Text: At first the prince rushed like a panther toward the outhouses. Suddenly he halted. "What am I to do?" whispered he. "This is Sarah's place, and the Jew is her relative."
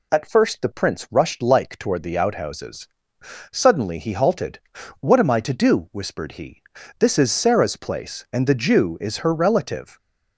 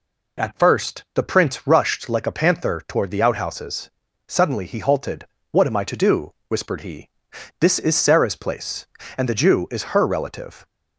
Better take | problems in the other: second | skips "a panther"; at 1.7 s

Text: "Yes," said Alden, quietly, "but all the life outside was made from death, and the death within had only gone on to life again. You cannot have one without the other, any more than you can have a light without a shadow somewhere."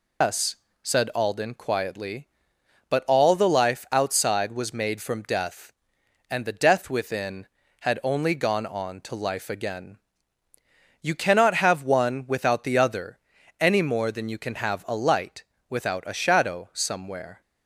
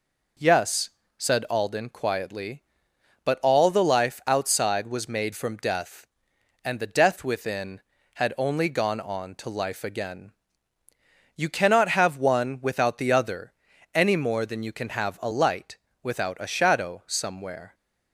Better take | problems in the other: second | loses the start of "Yes"; at 0.2 s; 165 ms // pauses between "light" and "without"; slight; at 15.4 s; 0.24 s long; slight in the second

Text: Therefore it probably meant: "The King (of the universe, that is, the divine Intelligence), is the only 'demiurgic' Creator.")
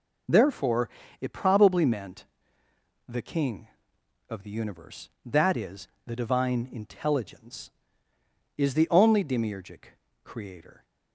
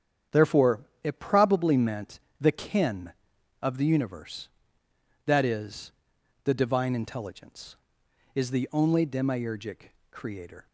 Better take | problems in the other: first | starts louder than the rest; strong; until 1.5 s; 8.5 dB // pauses between "Therefore" and "it"; slight; at 0.8 s; 0.22 s long; slight in the first // says "Kin" for "King"; at 2.5 s // pauses between "demiurgic" and "Creator"; slight; at 9.9 s; 0.20 s long; slight in the first

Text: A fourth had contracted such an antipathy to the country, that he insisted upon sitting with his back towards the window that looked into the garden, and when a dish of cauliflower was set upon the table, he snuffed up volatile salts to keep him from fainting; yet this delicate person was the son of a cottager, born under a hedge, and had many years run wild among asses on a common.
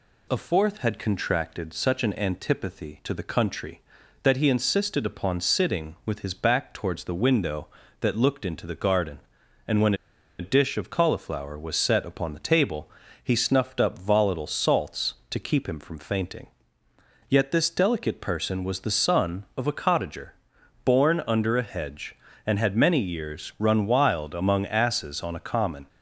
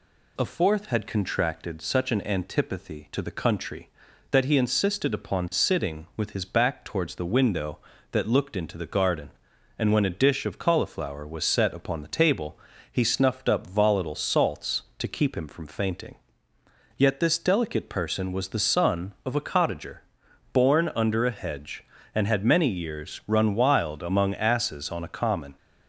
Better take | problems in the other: second | pauses between "when" and "a"; at 9.9 s; 0.45 s long

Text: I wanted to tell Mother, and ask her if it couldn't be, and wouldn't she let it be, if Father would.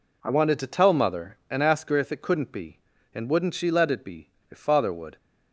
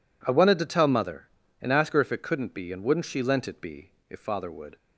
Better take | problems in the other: first | says "lent" for "let"; at 3.2 s

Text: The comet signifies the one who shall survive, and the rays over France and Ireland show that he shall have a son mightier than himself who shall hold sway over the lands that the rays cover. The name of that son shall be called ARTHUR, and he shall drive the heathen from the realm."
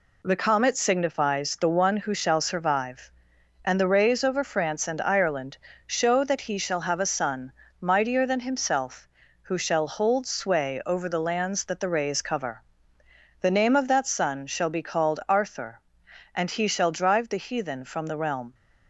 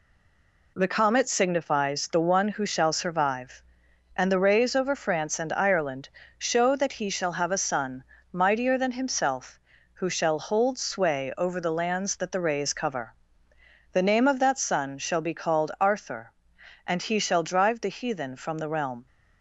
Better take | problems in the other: first | stays silent before the first word; slight; until 0.7 s; 0.7 s long // pauses between "Ireland" and "show"; slight; at 6.0 s; 0.30 s long; slight in the first // pauses between "son" and "mightier"; slight; at 8.0 s; 0.28 s long; slight in the first

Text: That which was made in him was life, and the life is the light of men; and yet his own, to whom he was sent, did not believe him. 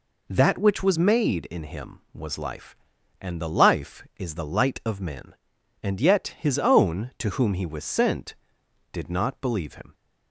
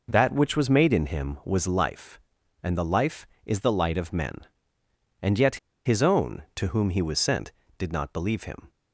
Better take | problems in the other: first | pauses between "yet" and "his"; slight; at 5.5 s; 0.28 s long

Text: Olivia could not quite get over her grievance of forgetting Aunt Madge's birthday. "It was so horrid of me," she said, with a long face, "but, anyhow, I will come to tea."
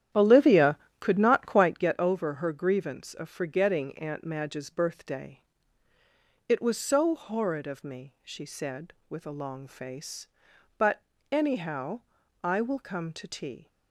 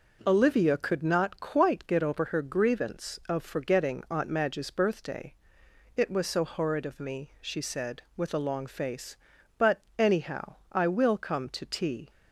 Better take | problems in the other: second | starts louder than the rest; strong; until 1.9 s; 11 dB

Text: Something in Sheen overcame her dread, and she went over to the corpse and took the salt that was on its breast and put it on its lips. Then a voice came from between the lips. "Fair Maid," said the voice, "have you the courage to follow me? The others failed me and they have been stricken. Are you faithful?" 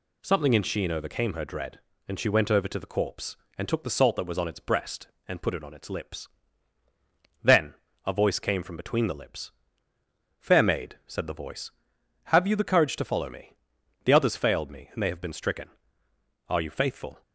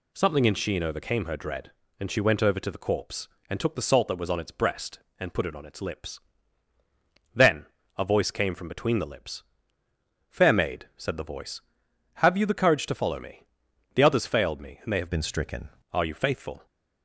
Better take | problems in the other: first | pauses between "Then" and "a"; slight; at 7.6 s; 0.32 s long; slight in the first // changes voice from "been" to "stricken"; from 15.1 to 15.6 s; 0.5 s long

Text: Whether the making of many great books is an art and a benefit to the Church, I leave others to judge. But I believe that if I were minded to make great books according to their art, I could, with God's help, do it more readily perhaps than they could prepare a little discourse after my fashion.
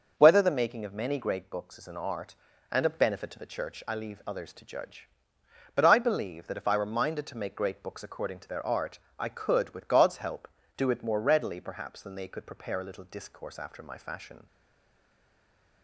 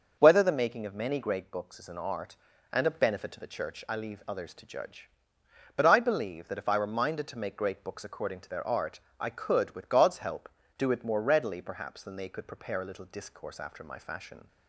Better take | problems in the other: second | starts louder than the rest; noticeable; until 1.1 s; 6 dB; noticeable in the second // stays silent after the last word; noticeable; from 14.4 s on; 1.4 s long

